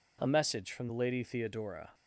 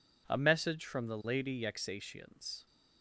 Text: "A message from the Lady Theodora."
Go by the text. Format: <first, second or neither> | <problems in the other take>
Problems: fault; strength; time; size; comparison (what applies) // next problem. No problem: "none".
first | says "Yexatians" for "Theodora"; at 1.6 s